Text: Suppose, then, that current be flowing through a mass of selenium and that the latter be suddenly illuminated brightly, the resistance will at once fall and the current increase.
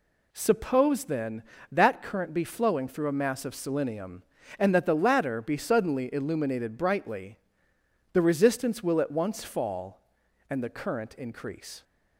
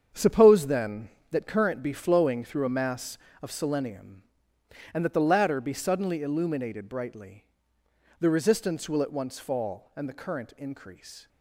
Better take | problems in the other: first | gets quieter; strong; throughout; 10.5 dB

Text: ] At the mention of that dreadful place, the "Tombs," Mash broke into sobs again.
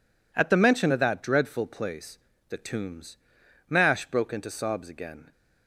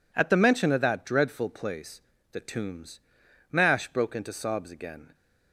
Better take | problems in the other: neither | none

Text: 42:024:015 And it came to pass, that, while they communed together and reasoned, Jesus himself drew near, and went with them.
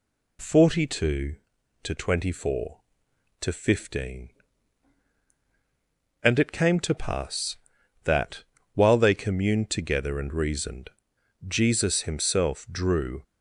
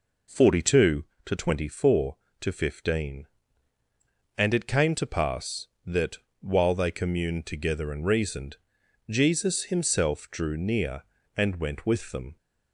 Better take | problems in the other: second | stops before "near and went with them"; at 13.2 s

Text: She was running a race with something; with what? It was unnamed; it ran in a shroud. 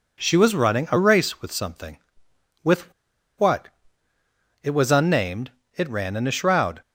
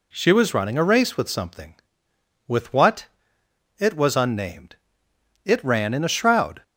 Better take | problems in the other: second | pauses between "with" and "what"; at 2.9 s; 0.45 s long

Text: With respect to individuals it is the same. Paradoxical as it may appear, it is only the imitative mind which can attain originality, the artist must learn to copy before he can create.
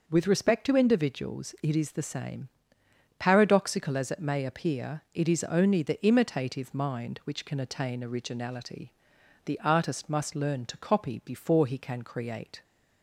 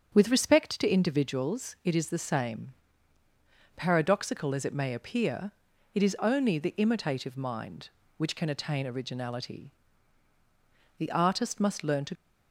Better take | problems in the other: first | starts louder than the rest; until 1.1 s; 7 dB // stops before "copy before he can create"; at 12.1 s

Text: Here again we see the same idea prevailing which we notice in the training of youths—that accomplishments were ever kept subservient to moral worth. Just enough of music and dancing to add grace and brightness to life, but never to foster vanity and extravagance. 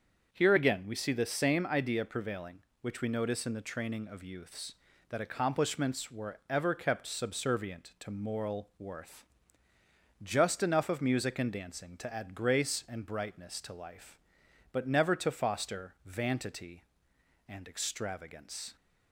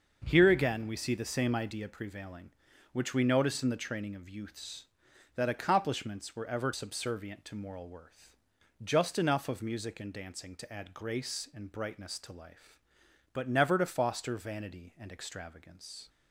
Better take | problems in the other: first | starts louder than the rest; noticeable; until 1.2 s; 6 dB; also in the first // skips "kept"; at 6.7 s

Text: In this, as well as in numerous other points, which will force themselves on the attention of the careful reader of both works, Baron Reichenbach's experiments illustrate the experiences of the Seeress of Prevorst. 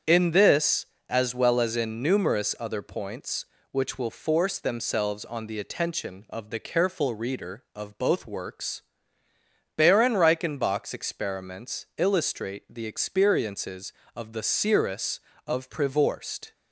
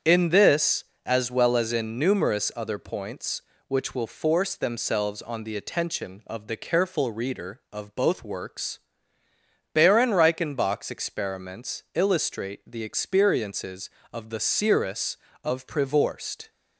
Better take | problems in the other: neither | starts louder than the rest; strong; the same in both

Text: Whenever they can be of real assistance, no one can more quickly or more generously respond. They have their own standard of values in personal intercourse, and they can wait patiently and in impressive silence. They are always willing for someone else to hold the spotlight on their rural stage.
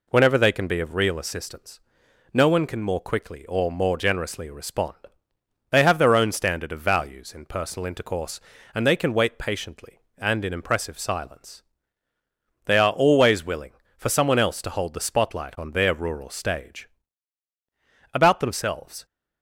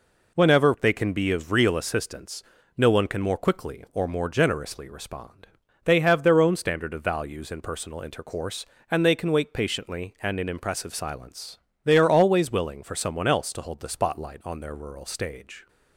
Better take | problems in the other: second | goes on to say "About themselves"; noticeable; from 18.1 s on; 0.92 s long

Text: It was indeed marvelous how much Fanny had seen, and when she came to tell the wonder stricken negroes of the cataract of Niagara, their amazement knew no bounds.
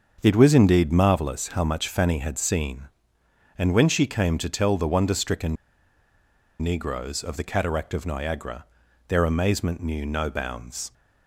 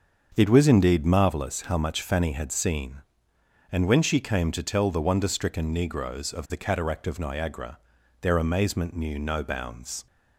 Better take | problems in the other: second | starts louder than the rest; until 1.2 s; 6.5 dB; also in the second // pauses between "stricken" and "negroes"; at 5.5 s; 1.0 s long

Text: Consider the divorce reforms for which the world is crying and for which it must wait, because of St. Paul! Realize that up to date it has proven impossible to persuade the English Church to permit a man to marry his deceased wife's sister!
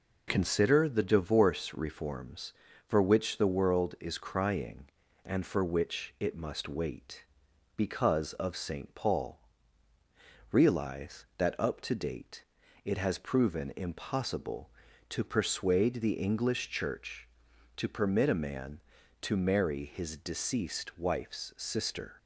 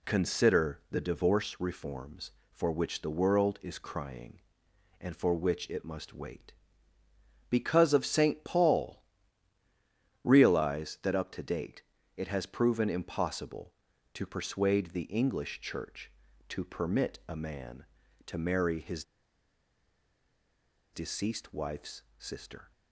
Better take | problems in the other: first | pauses between "date" and "it"; slight; at 11.8 s; 0.34 s long; also in the first // pauses between "his" and "deceased"; strong; at 19.0 s; 1.8 s long // pauses between "wife's" and "sister"; slight; at 22.0 s; 0.16 s long

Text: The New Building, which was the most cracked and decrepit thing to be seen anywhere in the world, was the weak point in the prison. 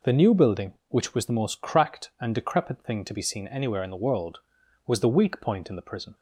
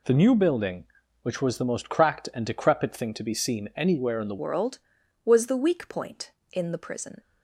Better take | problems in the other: first | changes voice at "world"; from 4.3 s on; 2.9 s long

